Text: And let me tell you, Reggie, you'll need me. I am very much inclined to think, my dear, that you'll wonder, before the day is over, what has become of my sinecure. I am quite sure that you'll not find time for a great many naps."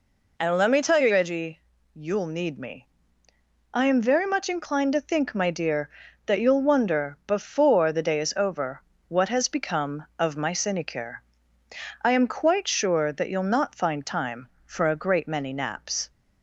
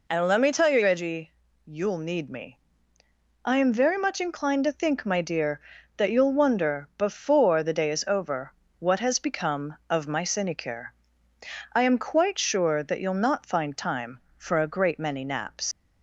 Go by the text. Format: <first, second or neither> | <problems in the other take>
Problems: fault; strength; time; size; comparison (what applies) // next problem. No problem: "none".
first | leaves "naps" unfinished; at 15.7 s; 110 ms